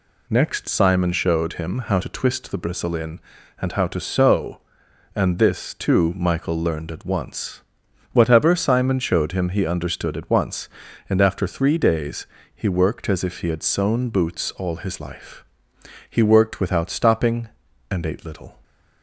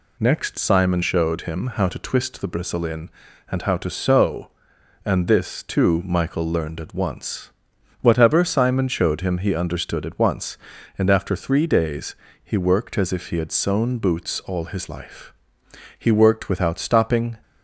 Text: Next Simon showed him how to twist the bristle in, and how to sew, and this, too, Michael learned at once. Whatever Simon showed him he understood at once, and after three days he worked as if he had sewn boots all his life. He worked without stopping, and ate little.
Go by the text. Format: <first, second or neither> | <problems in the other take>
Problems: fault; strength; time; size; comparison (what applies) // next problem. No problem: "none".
first | pauses between "days" and "he"; slight; at 12.1 s; 0.30 s long; slight in the first // stops before "and ate little"; at 17.4 s